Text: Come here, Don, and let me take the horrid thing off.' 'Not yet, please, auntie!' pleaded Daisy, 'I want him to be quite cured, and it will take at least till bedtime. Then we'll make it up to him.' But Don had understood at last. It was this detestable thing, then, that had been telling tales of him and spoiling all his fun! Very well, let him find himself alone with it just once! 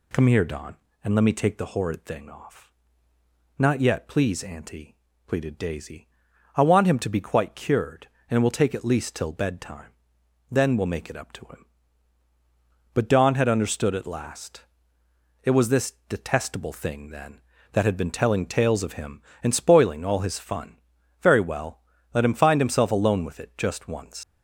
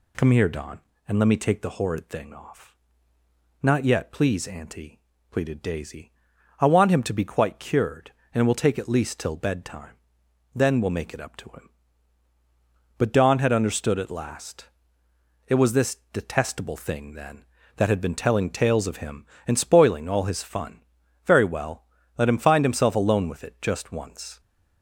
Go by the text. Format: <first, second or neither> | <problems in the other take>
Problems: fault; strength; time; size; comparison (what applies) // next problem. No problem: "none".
second | pauses between "this" and "detestable"; slight; at 15.9 s; 0.16 s long; slight in the second // leaves "once" unfinished; at 24.2 s; 125 ms